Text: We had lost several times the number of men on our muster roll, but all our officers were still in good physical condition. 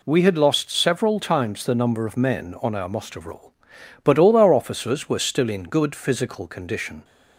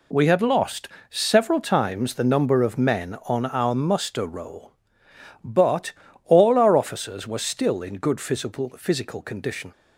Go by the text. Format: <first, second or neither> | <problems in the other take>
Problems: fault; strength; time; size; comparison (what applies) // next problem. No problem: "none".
first | pauses between "lost" and "several"; slight; at 0.8 s; 0.20 s long // pauses between "but" and "all"; slight; at 5.9 s; 0.32 s long // says "physical" twice; at 8.7 s